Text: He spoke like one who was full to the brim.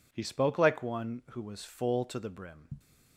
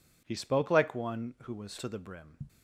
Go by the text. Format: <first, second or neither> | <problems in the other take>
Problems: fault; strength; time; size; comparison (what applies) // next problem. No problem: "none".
first | skips "full"; at 1.7 s